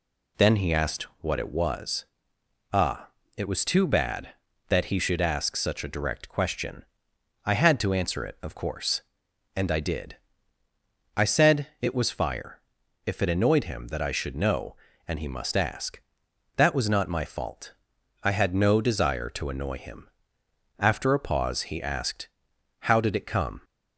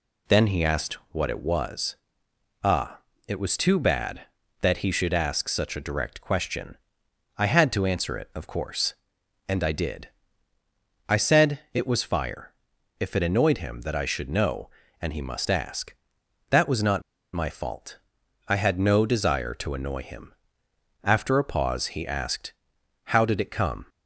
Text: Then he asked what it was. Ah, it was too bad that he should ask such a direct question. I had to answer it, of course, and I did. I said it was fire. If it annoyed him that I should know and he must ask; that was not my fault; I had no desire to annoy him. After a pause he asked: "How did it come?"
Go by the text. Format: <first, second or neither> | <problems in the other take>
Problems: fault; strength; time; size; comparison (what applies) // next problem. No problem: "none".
first | pauses between "not" and "my"; slight; at 17.0 s; 0.32 s long